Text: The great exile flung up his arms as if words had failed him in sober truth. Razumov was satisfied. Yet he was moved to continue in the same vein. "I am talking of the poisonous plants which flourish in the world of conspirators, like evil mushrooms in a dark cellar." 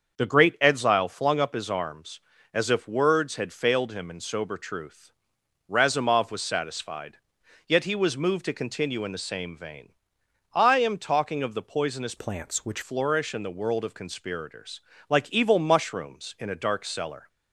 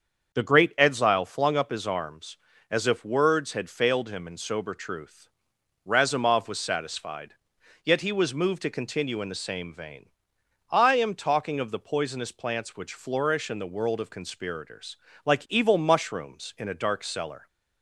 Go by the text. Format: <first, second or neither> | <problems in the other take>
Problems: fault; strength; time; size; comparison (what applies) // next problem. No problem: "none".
second | starts louder than the rest; until 1.2 s; 6.5 dB; also in the second // changes voice from "plants" to "which"; from 12.1 to 12.8 s; 0.7 s long